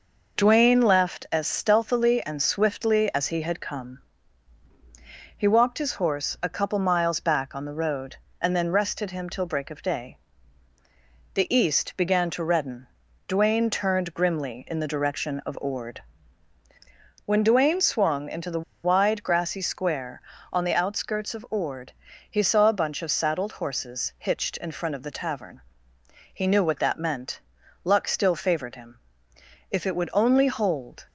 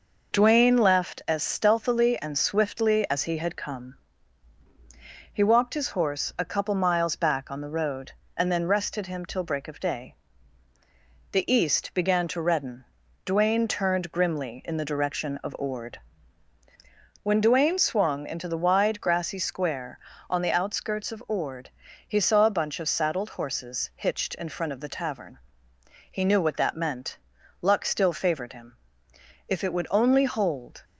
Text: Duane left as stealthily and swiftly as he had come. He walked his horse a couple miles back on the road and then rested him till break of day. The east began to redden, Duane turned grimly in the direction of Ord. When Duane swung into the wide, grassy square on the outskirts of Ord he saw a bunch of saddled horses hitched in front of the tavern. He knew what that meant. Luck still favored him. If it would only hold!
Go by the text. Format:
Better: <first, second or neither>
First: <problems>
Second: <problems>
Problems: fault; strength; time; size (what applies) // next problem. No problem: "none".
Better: second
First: pauses between "the" and "wide"; slight; at 18.6 s; 0.22 s long // pauses between "Ord" and "he"; at 21.9 s; 0.38 s long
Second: pauses between "Ord" and "he"; at 21.6 s; 0.38 s long